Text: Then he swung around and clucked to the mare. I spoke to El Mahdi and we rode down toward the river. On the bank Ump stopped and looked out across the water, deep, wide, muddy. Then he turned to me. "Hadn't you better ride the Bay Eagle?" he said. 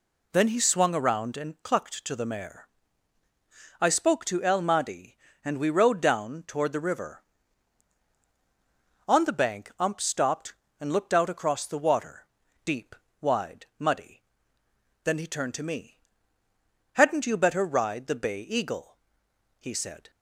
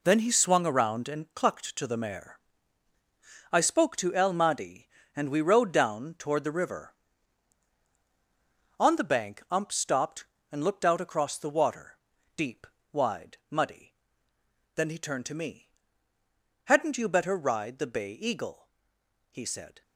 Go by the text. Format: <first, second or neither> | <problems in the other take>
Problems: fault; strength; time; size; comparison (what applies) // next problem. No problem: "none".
first | gets quieter; strong; throughout; 9.5 dB